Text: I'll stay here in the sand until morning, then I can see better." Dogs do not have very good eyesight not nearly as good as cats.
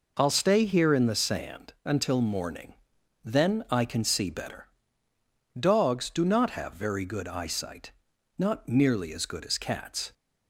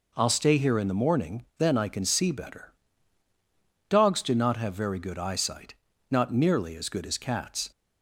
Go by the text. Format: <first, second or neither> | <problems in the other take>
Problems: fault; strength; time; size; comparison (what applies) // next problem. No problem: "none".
first | skips "sand until"; at 0.9 s // pauses between "eyesight" and "not"; at 5.7 s; 0.38 s long; also in the first